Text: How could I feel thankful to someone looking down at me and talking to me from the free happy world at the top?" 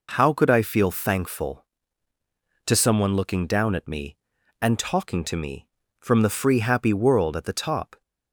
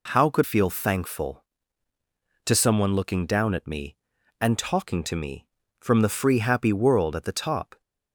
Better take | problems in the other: first | skips "I"; at 0.4 s

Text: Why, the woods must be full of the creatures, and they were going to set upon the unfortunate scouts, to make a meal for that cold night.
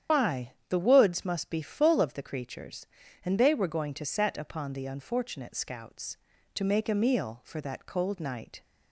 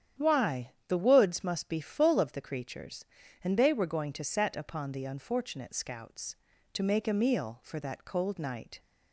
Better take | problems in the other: second | loses the start of "Why"; at 0.0 s; 115 ms // starts louder than the rest; strong; until 1.2 s; 9 dB; strong in the second

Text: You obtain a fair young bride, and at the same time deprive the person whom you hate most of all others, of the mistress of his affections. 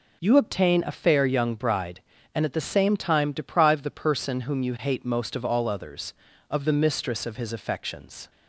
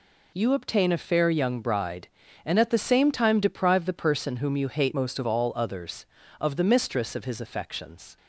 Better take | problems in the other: first | changes voice from "most" to "of"; from 4.9 to 5.2 s; 0.3 s long

